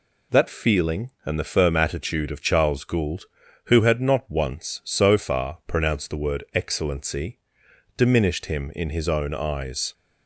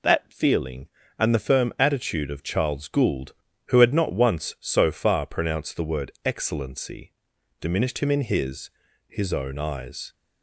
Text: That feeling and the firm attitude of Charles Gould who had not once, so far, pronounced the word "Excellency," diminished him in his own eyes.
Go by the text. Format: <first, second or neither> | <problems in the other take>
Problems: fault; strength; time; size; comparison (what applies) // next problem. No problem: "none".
first | says "his" twice; at 9.0 s